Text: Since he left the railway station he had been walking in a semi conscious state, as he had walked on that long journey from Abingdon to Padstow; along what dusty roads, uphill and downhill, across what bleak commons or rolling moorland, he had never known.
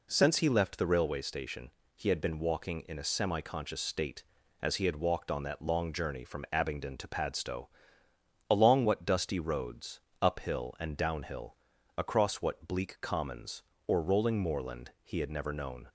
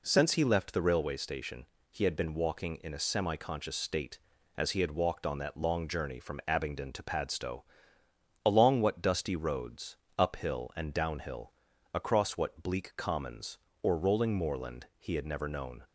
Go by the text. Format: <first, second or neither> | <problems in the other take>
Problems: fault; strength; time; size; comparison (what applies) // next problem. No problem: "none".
neither | pauses between "station" and "he"; slight; the same in both